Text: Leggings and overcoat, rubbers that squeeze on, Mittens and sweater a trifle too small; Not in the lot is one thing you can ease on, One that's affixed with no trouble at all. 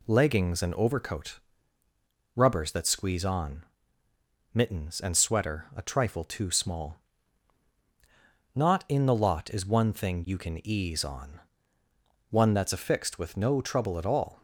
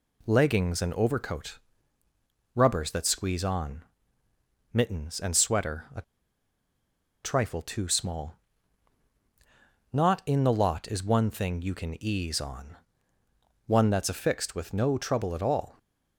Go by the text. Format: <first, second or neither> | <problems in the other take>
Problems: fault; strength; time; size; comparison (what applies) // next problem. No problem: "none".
first | pauses between "a" and "trifle"; at 6.0 s; 1.2 s long